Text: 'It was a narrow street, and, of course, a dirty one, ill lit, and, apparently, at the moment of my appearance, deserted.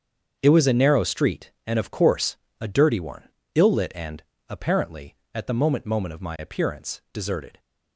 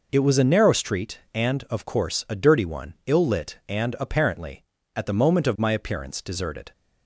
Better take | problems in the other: second | starts louder than the rest; strong; until 1.4 s; 7 dB // says "moment" twice; at 5.8 s

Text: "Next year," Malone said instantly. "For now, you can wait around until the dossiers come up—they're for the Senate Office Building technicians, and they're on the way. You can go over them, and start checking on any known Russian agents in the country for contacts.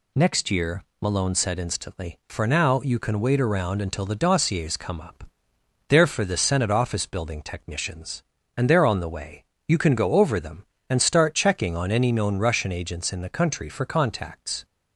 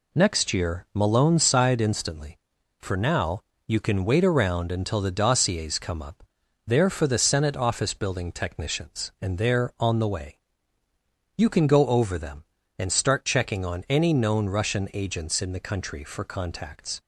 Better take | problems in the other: first | says "sighed" for "said"; at 1.3 s

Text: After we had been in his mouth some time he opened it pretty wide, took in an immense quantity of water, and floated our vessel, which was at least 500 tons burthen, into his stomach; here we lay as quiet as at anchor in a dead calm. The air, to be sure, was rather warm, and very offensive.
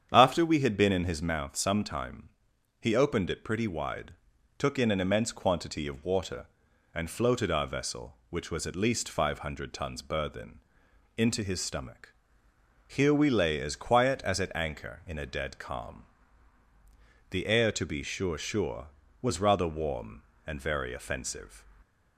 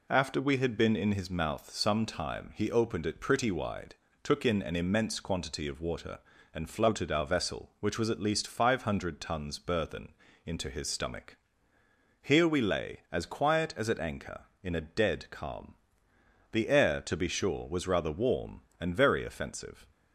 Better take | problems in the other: second | starts louder than the rest; strong; until 1.1 s; 8.5 dB // pauses between "time" and "he"; noticeable; at 2.2 s; 0.52 s long // says "sure" twice; at 18.3 s

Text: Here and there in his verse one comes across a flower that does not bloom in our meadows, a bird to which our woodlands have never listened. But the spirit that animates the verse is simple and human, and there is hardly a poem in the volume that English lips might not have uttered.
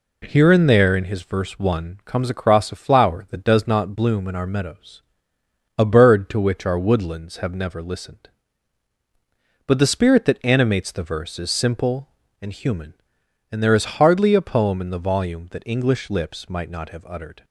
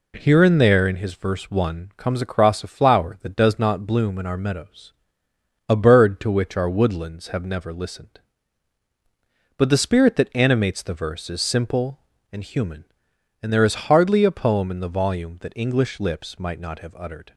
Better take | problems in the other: neither | none

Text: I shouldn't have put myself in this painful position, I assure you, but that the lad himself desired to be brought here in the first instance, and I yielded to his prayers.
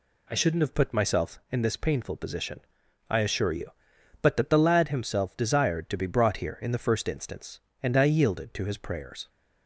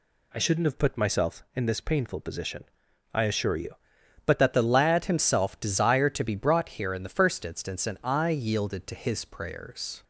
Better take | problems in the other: first | changes voice at "that"; from 4.3 s on; 5.7 s long

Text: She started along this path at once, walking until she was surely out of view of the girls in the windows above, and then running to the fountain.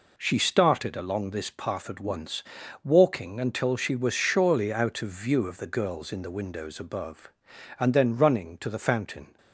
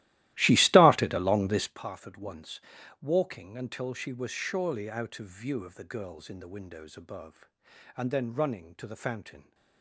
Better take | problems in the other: first | starts louder than the rest; strong; until 1.8 s; 16 dB

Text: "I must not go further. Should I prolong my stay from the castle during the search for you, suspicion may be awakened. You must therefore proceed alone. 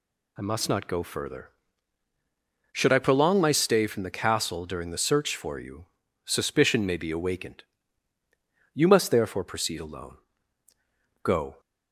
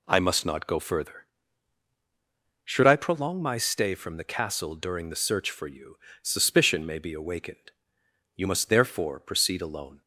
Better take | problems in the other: second | goes on to say "Go"; slight; from 11.2 s on; 0.36 s long

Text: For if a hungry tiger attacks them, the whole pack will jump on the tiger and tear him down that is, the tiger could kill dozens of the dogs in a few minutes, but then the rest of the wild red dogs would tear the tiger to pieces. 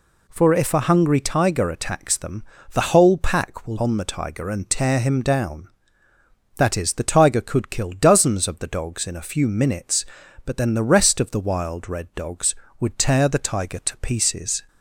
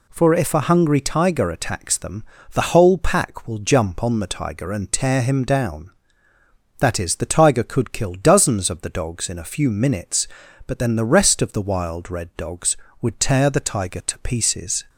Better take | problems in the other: second | skips "jump"; at 3.7 s

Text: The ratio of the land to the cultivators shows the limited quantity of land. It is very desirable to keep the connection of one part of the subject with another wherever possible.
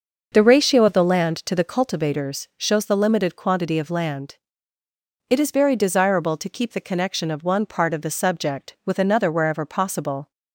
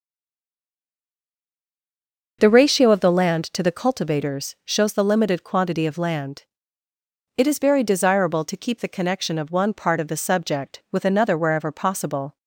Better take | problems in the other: first | stays silent before the first word; until 2.4 s; 2.4 s long // starts louder than the rest; noticeable; until 3.4 s; 6 dB; noticeable in the first

